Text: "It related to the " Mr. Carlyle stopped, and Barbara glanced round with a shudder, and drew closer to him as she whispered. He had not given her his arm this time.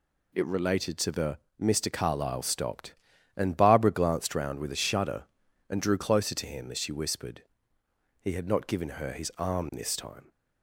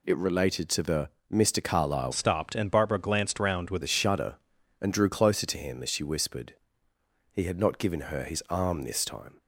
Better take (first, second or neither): first